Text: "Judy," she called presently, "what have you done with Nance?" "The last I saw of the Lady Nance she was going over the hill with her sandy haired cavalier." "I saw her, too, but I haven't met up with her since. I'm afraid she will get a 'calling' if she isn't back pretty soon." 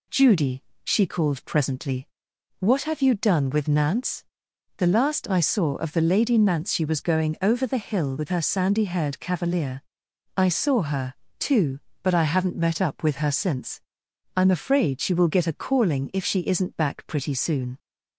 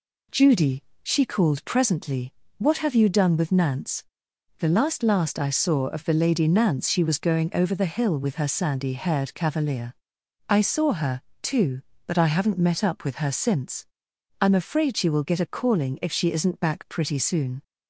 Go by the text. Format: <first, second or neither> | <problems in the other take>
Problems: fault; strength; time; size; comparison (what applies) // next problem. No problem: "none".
first | says "last" twice; at 5.0 s